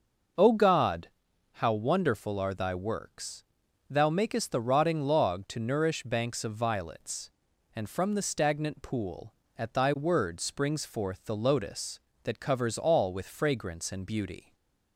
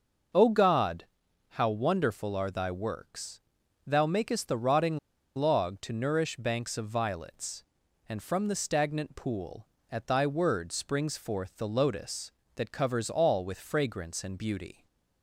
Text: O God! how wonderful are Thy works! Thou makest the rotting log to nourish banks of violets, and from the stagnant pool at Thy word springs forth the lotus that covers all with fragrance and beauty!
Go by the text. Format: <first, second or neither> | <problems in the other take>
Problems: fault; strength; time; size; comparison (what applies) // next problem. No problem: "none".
first | starts louder than the rest; noticeable; until 1.8 s; 6 dB; noticeable in the first // pauses between "rotting" and "log"; at 4.9 s; 0.37 s long // stays silent after the last word; slight; from 14.7 s on; 0.5 s long; slight in the first